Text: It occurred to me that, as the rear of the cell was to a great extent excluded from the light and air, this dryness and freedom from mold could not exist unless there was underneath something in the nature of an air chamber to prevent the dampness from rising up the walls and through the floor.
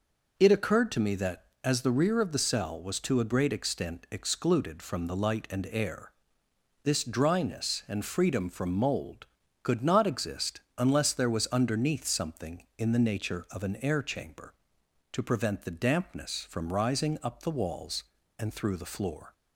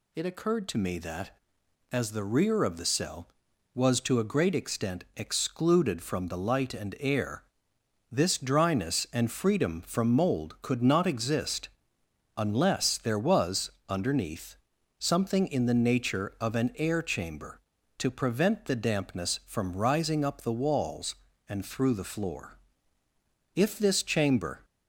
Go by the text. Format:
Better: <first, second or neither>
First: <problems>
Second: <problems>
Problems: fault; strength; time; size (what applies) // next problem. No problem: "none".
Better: first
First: pauses between "exist" and "unless"; slight; at 10.6 s; 0.18 s long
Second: pauses between "exist" and "unless"; noticeable; at 11.6 s; 0.68 s long // pauses between "was" and "underneath"; slight; at 13.7 s; 0.18 s long // pauses between "underneath" and "something"; at 14.5 s; 0.42 s long // goes on to say "If this chamber"; noticeable; from 23.5 s on; 1.1 s long